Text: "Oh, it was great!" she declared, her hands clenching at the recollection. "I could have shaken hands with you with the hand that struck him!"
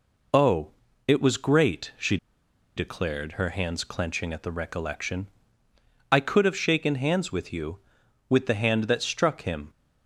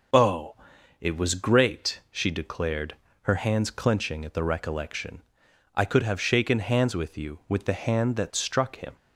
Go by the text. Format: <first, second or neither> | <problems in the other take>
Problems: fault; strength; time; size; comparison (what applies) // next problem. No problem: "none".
second | pauses between "she" and "declared"; noticeable; at 2.1 s; 0.60 s long